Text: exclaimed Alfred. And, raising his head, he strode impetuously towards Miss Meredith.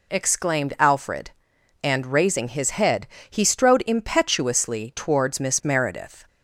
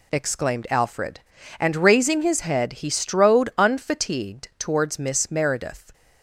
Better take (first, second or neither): first